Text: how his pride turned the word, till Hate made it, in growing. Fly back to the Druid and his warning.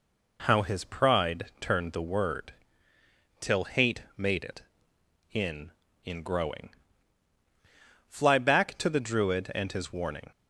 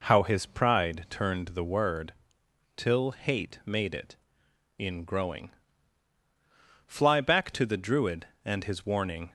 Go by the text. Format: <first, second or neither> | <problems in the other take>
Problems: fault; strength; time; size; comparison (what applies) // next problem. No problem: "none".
second | pauses between "Hate" and "made"; slight; at 4.0 s; 0.16 s long // says "in" twice; at 6.0 s